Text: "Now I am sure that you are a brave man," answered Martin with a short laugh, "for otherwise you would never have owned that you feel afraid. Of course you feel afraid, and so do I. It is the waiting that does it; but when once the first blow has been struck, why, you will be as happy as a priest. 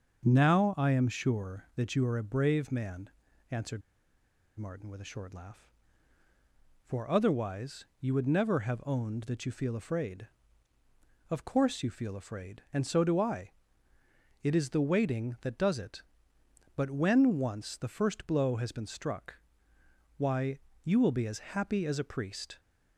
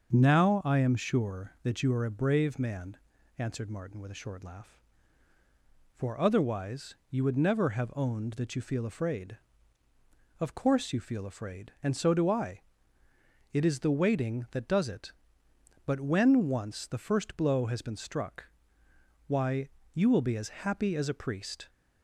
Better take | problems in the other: second | starts louder than the rest; until 1.2 s; 6.5 dB; also in the second // pauses between "answered" and "Martin"; noticeable; at 3.8 s; 0.77 s long // pauses between "otherwise" and "you"; slight; at 7.8 s; 0.16 s long; slight in the second

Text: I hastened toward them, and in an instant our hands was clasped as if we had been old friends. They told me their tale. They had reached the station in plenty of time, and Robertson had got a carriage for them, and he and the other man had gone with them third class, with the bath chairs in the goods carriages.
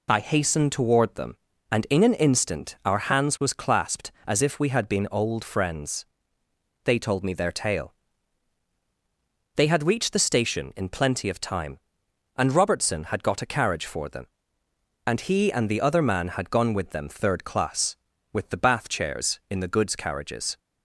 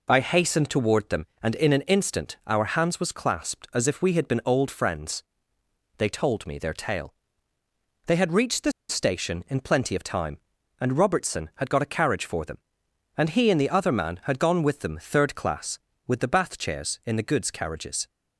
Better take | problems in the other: first | pauses between "the" and "station"; slight; at 8.7 s; 0.18 s long

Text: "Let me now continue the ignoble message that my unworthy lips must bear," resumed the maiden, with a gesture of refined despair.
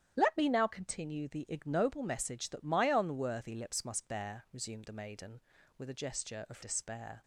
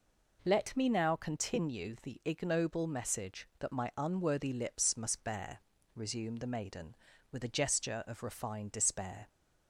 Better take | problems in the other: second | starts louder than the rest; strong; until 1.1 s; 10 dB // skips "refined"; at 6.6 s

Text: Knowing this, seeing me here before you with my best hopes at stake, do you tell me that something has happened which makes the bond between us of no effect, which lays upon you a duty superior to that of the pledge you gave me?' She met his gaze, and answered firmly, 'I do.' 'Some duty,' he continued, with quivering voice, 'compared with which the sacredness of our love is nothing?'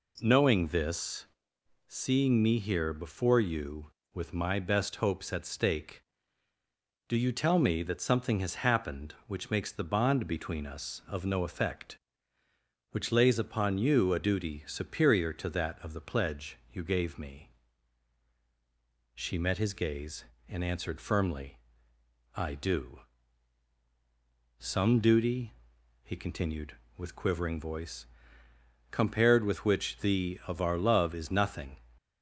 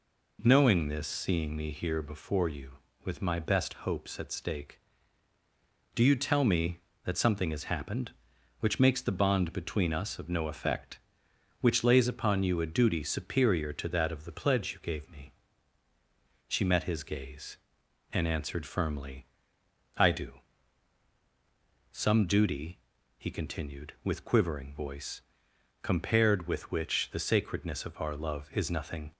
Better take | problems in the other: second | skips "sacredness"; at 30.4 s

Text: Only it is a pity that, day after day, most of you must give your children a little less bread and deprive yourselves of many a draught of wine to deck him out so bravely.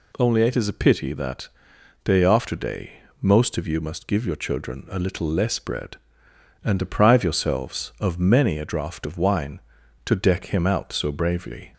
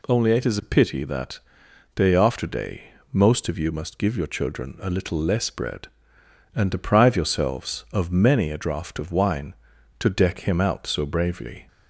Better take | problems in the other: neither | none

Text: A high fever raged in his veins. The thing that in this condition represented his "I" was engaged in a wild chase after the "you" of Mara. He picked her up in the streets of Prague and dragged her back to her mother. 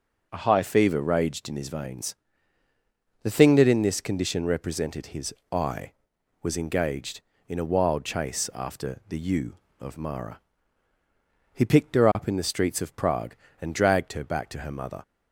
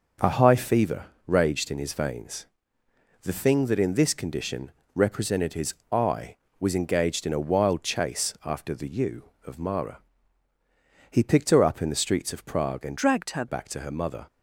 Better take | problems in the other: first | starts louder than the rest; until 1.4 s; 6.5 dB // pauses between "fever" and "raged"; slight; at 1.0 s; 0.22 s long // pauses between "condition" and "represented"; slight; at 4.7 s; 0.22 s long // pauses between "his" and "I"; slight; at 5.7 s; 0.20 s long; slight in the first // changes voice from "dragged" to "her"; from 12.9 to 13.4 s; 0.5 s long

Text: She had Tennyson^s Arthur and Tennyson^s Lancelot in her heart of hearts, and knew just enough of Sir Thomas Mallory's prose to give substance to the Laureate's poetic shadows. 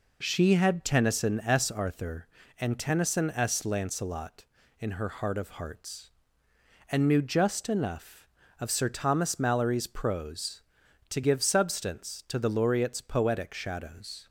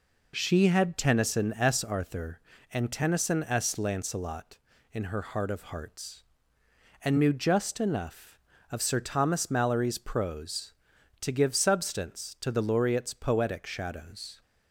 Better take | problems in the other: neither | none

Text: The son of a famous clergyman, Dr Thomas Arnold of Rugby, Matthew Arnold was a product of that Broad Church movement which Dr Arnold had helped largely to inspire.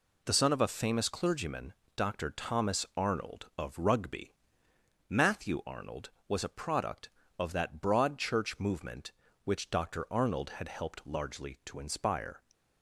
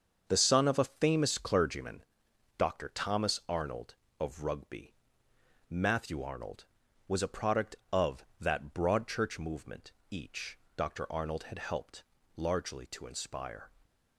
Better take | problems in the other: first | starts louder than the rest; until 1.2 s; 7 dB // says "each" for "which"; at 10.1 s // pauses between "helped" and "largely"; slight; at 12.0 s; 0.32 s long

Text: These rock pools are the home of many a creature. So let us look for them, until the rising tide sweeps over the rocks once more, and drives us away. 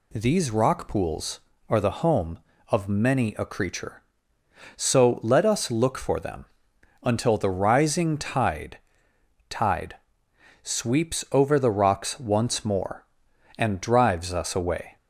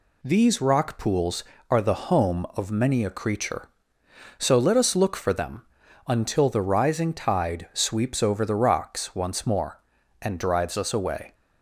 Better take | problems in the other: second | says "tide" twice; at 9.4 s

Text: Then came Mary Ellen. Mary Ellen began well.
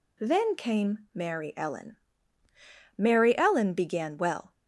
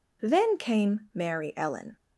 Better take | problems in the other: first | stops before "Mary Ellen began well"; at 1.9 s

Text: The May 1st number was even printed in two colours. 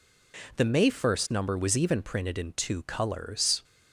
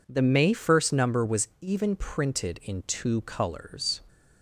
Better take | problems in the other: neither | none

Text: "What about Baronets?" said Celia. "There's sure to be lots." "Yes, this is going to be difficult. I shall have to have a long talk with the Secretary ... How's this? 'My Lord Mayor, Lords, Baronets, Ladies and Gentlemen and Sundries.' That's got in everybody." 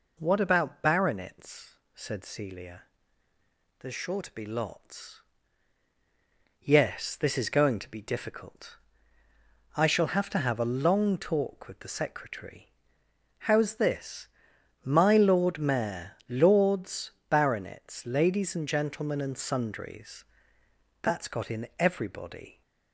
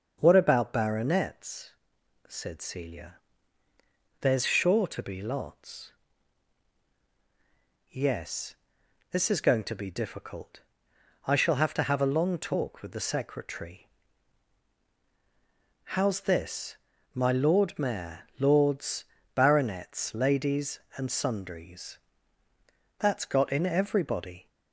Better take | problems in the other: first | starts louder than the rest; until 1.2 s; 6.5 dB // skips "Gentlemen and"; at 21.1 s

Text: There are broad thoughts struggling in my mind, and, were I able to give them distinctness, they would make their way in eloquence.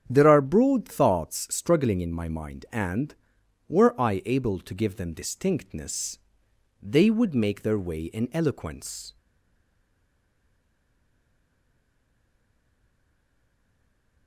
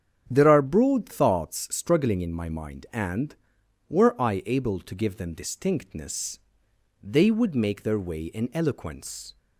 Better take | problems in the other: second | starts louder than the rest; strong; until 1.0 s; 8.5 dB; strong in the second // stays silent after the last word; strong; from 9.1 s on; 5.1 s long

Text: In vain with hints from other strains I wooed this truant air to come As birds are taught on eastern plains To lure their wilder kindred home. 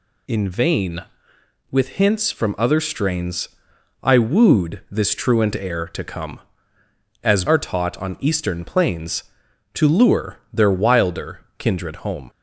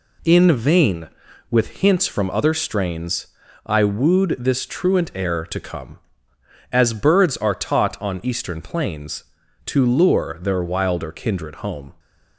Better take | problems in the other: second | pauses between "strains" and "I"; noticeable; at 3.4 s; 0.56 s long; slight in the second // skips "birds"; at 7.4 s // pauses between "wilder" and "kindred"; slight; at 11.3 s; 0.18 s long

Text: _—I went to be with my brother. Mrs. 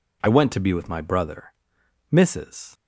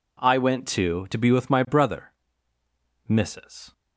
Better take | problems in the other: first | says "to" twice; at 1.0 s

